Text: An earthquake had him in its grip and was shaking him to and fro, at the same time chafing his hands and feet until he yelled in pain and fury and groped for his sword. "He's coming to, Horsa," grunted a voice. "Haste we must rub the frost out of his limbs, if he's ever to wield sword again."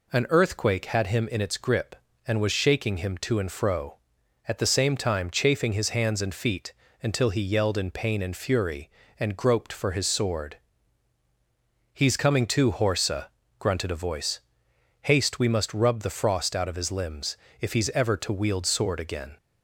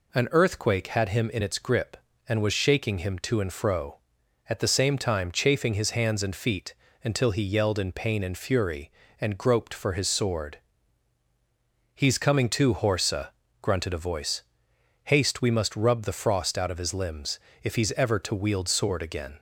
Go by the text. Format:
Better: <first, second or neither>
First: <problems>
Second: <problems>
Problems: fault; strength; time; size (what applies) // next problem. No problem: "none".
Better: neither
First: pauses between "feet" and "until"; slight; at 6.7 s; 0.30 s long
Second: pauses between "feet" and "until"; slight; at 6.7 s; 0.30 s long